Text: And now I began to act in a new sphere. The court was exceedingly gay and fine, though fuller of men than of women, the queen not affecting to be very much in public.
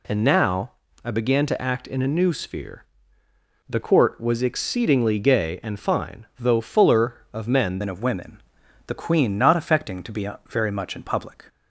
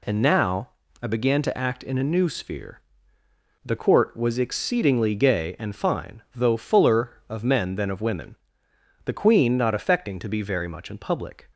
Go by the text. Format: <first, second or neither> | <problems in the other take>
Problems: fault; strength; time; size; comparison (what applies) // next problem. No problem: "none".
second | pauses between "now" and "I"; slight; at 0.7 s; 0.32 s long; slight in the second // changes voice at "than"; from 7.8 s on; 3.6 s long // pauses between "be" and "very"; slight; at 10.2 s; 0.20 s long